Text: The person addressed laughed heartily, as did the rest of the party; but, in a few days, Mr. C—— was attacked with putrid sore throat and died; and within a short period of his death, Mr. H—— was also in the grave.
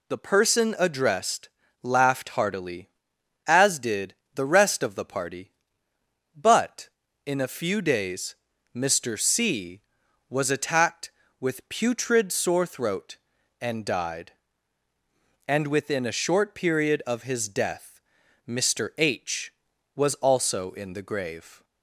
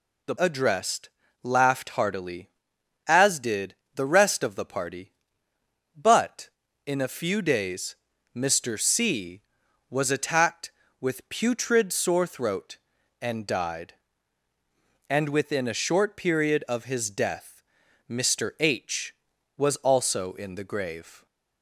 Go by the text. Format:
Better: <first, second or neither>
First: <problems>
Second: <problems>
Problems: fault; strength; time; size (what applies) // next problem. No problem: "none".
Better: first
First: pauses between "addressed" and "laughed"; slight; at 1.4 s; 0.32 s long // pauses between "did" and "the"; slight; at 4.1 s; 0.22 s long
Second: skips "person"; at 0.3 s // pauses between "addressed" and "laughed"; slight; at 1.0 s; 0.32 s long // pauses between "did" and "the"; slight; at 3.7 s; 0.22 s long